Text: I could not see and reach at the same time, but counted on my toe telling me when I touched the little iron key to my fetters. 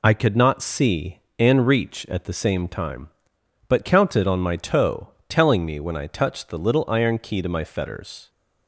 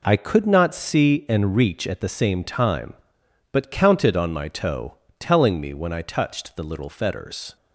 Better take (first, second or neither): first